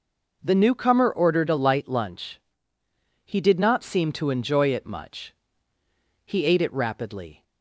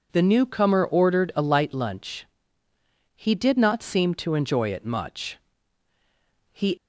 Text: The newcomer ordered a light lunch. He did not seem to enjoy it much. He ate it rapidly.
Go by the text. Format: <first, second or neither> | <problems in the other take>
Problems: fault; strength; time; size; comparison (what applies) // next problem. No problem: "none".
first | stops before "ate it rapidly"; at 6.7 s